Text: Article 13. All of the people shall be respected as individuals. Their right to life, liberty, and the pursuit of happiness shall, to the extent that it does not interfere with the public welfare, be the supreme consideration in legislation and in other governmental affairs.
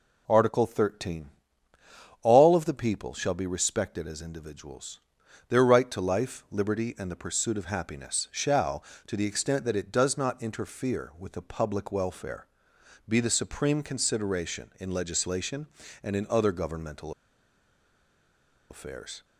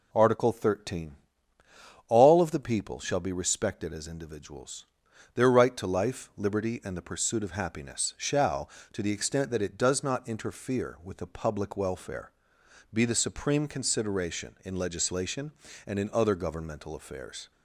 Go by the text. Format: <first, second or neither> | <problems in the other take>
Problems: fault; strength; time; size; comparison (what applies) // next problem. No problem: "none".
second | pauses between "governmental" and "affairs"; strong; at 17.1 s; 1.5 s long